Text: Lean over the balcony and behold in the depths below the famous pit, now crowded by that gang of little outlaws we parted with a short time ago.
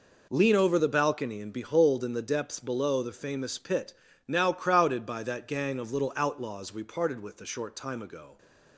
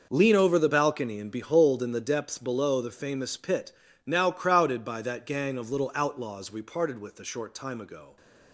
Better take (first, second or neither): first